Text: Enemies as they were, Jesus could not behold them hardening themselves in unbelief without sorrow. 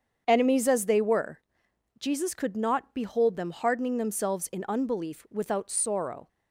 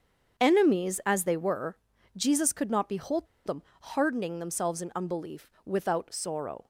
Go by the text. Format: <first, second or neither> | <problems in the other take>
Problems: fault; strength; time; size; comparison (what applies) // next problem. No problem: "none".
first | starts louder than the rest; strong; until 1.4 s; 7 dB; strong in the first // pauses between "behold" and "them"; slight; at 3.2 s; 0.18 s long // pauses between "them" and "hardening"; slight; at 3.6 s; 0.20 s long // pauses between "unbelief" and "without"; slight; at 5.4 s; 0.16 s long